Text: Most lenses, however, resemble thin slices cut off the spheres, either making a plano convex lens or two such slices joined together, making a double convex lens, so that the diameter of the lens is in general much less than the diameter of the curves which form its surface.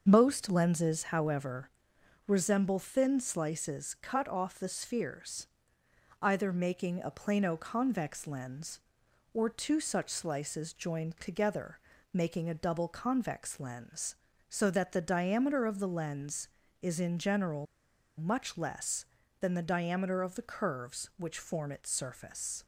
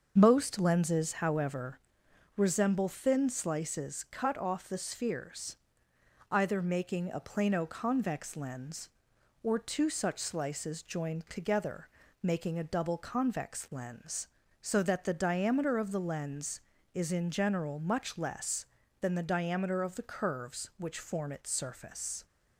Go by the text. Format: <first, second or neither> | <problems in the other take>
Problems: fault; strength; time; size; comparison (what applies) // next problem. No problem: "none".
second | starts louder than the rest; until 1.1 s; 6.5 dB; also in the second // pauses between "general" and "much"; noticeable; at 17.6 s; 0.53 s long